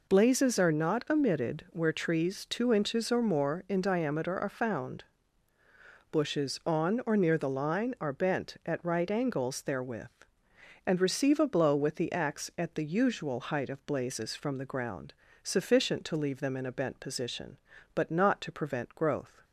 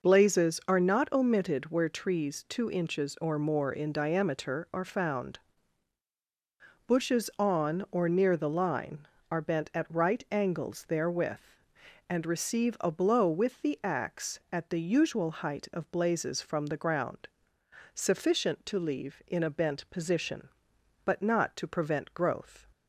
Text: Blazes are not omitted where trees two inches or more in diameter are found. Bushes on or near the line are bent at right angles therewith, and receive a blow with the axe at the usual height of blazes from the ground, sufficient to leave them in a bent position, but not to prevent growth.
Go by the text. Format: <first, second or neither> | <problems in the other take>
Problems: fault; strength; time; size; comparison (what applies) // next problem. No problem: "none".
first | skips "them"; at 19.2 s